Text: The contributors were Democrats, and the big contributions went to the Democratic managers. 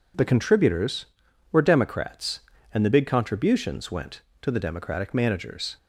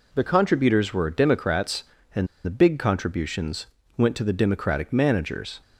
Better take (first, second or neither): first